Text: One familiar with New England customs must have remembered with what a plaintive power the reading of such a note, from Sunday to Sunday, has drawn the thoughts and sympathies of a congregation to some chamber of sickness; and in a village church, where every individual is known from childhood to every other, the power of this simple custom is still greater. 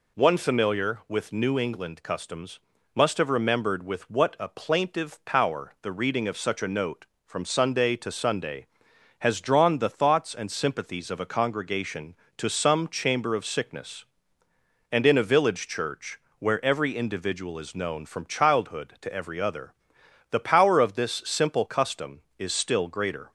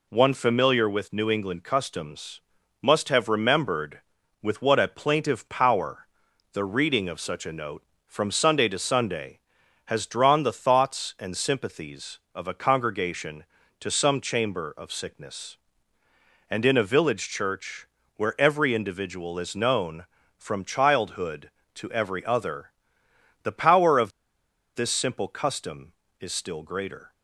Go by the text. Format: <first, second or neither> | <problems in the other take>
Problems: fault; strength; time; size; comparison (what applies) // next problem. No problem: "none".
first | pauses between "customs" and "must"; at 2.3 s; 0.40 s long; slight in the first // pauses between "power" and "the"; noticeable; at 6.0 s; 0.46 s long // pauses between "of" and "this"; noticeable; at 24.1 s; 0.64 s long